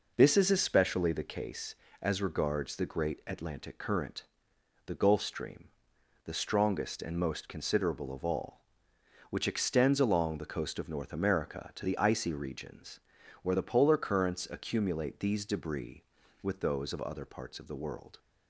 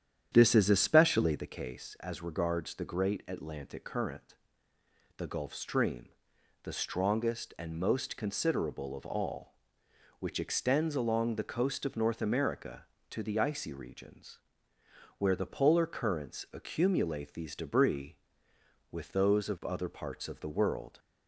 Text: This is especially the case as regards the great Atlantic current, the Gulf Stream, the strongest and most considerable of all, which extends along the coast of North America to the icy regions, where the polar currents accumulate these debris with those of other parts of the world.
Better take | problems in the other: first | starts louder than the rest; strong; until 1.6 s; 9.5 dB

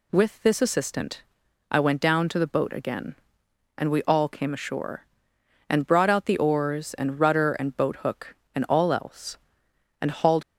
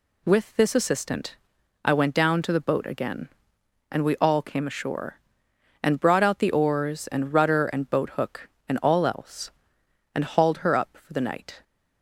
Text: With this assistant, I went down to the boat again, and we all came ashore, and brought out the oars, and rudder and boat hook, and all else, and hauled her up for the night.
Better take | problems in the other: second | stops before "her up for the night"; at 10.4 s

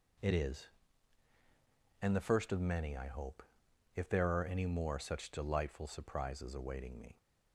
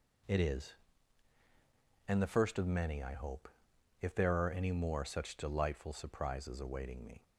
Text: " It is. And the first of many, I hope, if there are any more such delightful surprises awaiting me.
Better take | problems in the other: neither | none

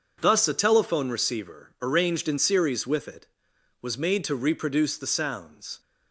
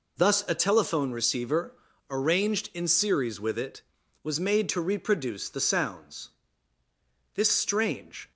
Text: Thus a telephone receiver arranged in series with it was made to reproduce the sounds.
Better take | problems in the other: first | pauses between "receiver" and "arranged"; slight; at 1.7 s; 0.36 s long // goes on to say "This strange"; noticeable; from 7.3 s on; 0.96 s long

